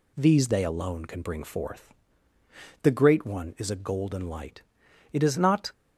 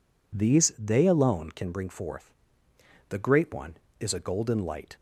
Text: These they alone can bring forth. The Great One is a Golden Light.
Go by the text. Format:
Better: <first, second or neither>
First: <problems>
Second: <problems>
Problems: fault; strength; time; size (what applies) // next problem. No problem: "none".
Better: second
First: goes on to say "It is not"; from 5.1 s on; 0.58 s long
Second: none